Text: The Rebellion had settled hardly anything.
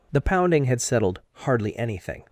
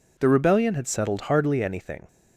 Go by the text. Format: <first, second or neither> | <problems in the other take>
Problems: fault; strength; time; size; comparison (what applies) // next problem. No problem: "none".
second | says "Pounding" for "Rebellion"; at 0.1 s